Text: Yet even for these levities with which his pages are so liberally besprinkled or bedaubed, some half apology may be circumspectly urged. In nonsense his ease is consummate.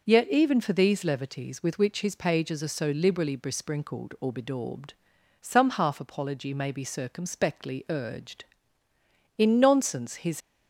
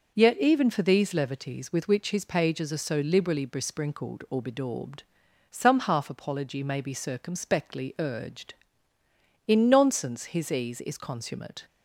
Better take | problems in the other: second | stops before "ease is consummate"; at 10.4 s

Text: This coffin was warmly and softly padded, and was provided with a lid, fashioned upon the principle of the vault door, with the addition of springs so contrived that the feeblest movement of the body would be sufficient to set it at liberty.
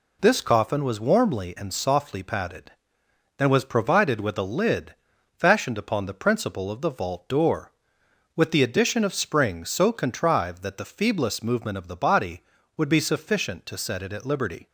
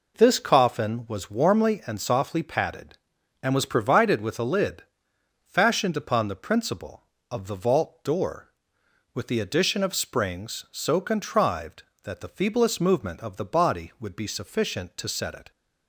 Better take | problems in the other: first | stops before "at liberty"; at 15.5 s

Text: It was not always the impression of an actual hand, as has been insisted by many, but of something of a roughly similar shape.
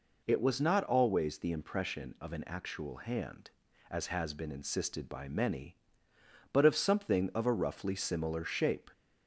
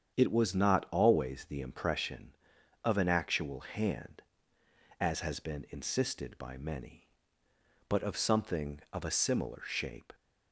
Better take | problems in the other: first | starts louder than the rest; strong; until 1.2 s; 8 dB // skips "roughly"; at 9.0 s

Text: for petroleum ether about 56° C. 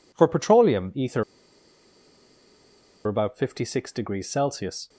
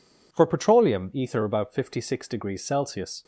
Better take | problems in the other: second | pauses between "ether" and "about"; strong; at 1.2 s; 1.8 s long

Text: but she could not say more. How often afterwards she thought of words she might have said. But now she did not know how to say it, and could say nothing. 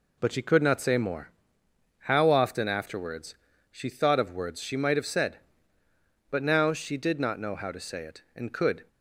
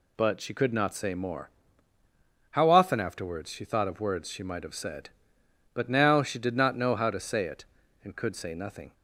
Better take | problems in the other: second | pauses between "afterwards" and "she"; slight; at 3.3 s; 0.34 s long // stops before "say nothing"; at 8.8 s

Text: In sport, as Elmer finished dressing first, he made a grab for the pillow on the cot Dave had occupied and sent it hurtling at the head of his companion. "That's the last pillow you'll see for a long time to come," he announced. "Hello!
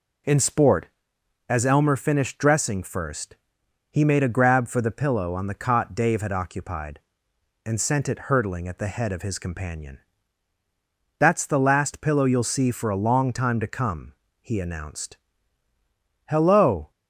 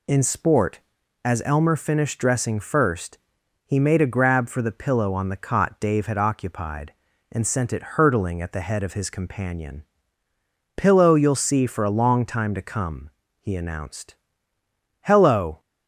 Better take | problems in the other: first | skips "That's the last"; at 10.2 s

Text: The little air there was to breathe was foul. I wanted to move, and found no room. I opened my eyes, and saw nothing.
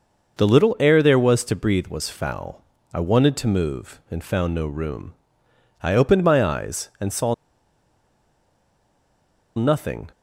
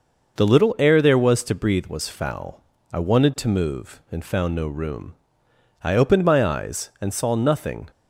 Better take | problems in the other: second | pauses between "saw" and "nothing"; strong; at 7.3 s; 2.2 s long

